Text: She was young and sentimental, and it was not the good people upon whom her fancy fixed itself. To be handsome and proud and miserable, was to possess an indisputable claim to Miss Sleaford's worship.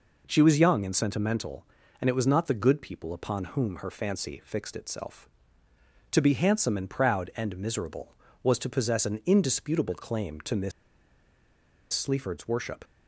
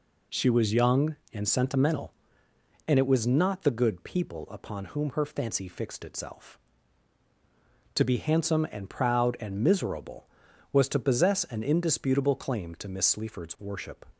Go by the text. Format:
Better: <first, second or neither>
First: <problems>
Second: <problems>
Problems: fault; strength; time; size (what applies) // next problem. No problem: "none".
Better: second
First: pauses between "Miss" and "Sleaford's"; at 10.7 s; 1.2 s long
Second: none